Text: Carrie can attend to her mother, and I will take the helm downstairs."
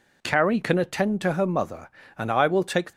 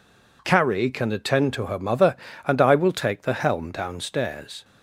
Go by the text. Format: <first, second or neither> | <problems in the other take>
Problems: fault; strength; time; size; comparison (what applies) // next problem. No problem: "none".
second | stops before "the helm downstairs"; at 2.9 s